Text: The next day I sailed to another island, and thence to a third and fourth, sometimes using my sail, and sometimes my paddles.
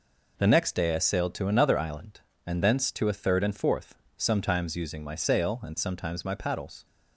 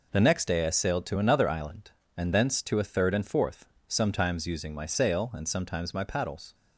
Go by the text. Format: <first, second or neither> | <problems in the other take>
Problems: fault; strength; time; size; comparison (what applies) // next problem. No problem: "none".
neither | none